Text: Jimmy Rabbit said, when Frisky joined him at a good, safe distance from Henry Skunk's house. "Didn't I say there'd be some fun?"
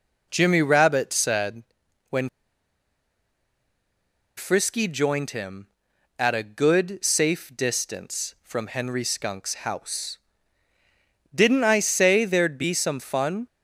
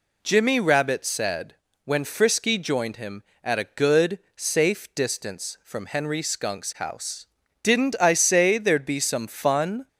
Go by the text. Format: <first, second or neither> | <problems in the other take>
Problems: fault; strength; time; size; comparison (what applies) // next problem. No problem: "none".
second | pauses between "when" and "Frisky"; strong; at 2.2 s; 2.0 s long